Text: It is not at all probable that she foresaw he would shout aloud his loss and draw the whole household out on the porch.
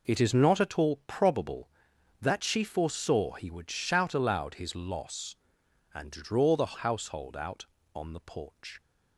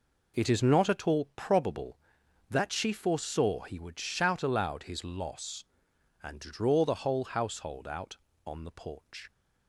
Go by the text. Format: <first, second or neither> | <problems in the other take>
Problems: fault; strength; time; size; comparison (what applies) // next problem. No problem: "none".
second | skips "whole"; at 6.7 s